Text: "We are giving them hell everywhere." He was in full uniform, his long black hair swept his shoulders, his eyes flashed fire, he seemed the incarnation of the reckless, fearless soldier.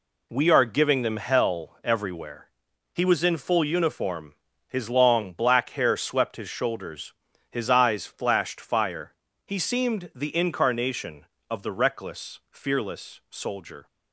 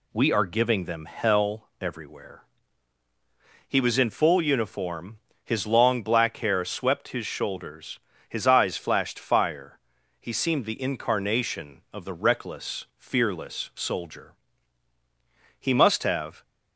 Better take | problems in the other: first | goes on to say "He must have"; noticeable; from 15.6 s on; 0.82 s long

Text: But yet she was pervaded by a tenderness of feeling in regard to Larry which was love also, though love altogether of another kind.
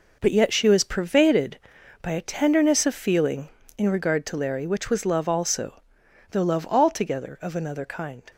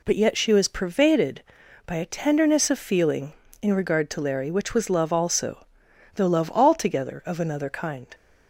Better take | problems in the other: second | gets quieter; strong; throughout; 9.5 dB

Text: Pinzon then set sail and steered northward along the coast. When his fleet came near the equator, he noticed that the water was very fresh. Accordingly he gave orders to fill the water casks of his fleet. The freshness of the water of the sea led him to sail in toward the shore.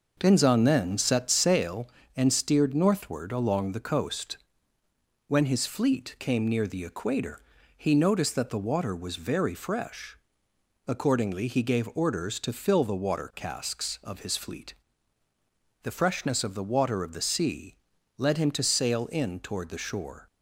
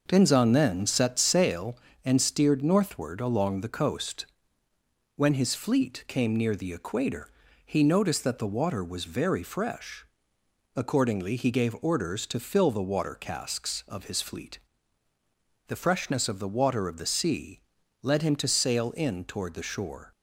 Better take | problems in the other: neither | pauses between "sea" and "led"; the same in both

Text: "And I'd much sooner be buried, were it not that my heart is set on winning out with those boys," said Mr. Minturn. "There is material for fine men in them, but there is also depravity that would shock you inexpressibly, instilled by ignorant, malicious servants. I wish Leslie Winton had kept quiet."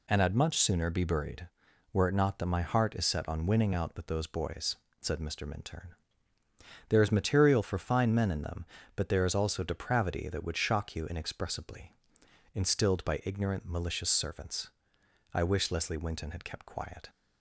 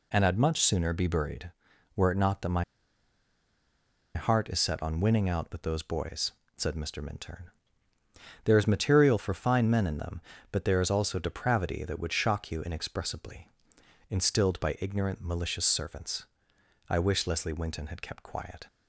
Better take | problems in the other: first | pauses between "my" and "heart"; strong; at 2.6 s; 1.5 s long

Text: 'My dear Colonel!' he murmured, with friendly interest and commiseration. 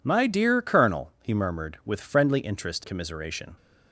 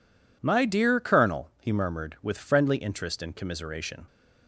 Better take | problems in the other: second | skips "and"; at 2.8 s

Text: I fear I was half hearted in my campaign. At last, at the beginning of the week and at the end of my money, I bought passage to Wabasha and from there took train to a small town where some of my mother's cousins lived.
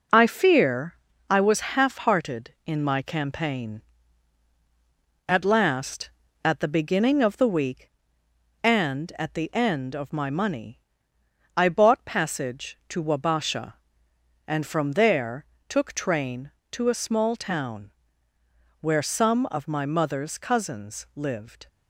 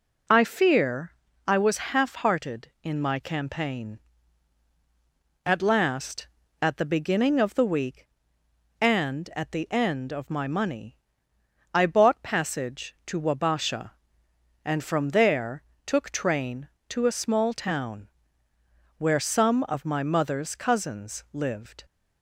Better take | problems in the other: second | gets quieter; noticeable; throughout; 5.5 dB // pauses between "fear" and "I"; slight; at 0.9 s; 0.34 s long; slight in the second // pauses between "there" and "took"; slight; at 15.4 s; 0.22 s long; slight in the second // pauses between "town" and "where"; noticeable; at 17.9 s; 0.88 s long; noticeable in the second

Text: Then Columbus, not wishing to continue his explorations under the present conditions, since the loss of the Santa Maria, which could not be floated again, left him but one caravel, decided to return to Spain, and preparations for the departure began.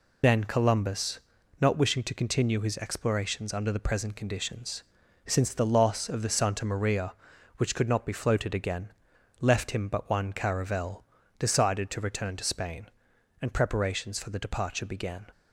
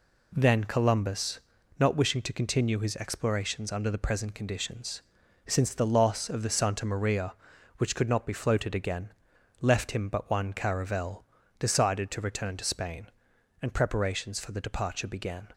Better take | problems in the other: second | loses the start of "Then"; at 0.2 s; 115 ms

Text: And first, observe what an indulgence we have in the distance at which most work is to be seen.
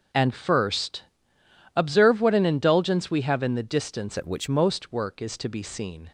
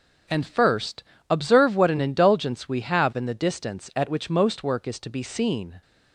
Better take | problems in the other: second | starts louder than the rest; until 1.8 s; 6.5 dB; also in the second // changes voice from "at" to "which"; from 4.1 to 4.4 s; 0.3 s long

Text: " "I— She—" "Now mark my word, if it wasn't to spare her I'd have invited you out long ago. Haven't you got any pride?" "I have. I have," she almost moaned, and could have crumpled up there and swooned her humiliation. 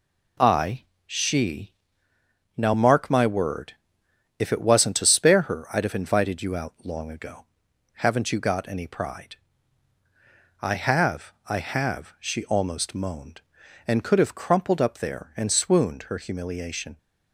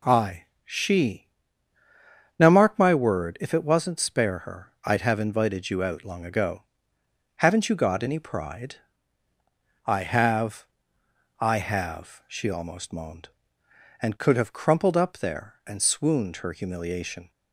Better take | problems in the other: first | skips "to"; at 4.0 s

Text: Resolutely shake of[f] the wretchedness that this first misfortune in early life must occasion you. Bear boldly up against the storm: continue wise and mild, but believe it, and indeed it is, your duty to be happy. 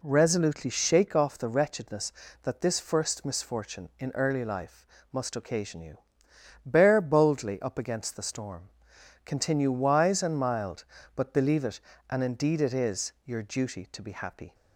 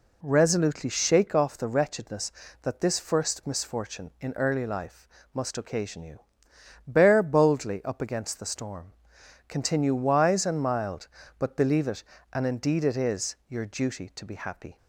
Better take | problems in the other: neither | pauses between "life" and "must"; slight; the same in both

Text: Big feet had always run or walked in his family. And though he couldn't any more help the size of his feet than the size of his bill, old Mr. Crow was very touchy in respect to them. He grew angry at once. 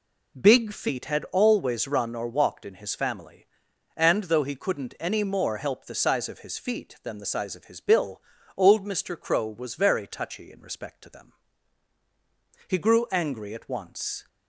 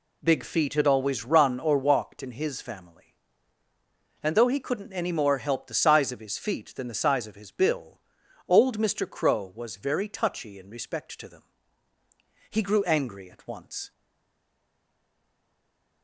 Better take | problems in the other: first | stays silent after the last word; from 13.9 s on; 2.1 s long

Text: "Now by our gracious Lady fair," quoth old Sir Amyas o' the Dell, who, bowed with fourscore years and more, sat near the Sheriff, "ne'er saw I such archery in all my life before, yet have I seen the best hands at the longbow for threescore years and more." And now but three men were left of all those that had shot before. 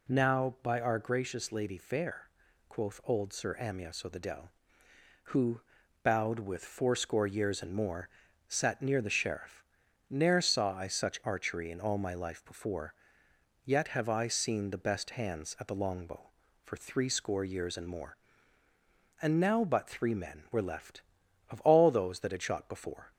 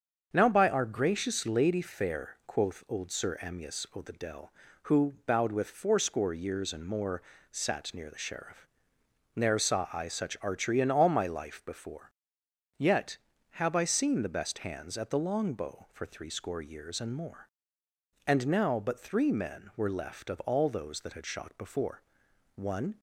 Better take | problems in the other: first | starts louder than the rest; until 1.3 s; 7 dB // goes on to say "One"; slight; from 22.5 s on; 0.46 s long

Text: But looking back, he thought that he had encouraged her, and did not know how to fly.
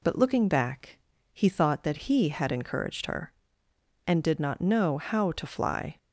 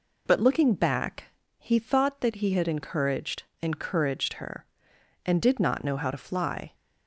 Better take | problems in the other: first | says "encouraged" twice; at 3.6 s

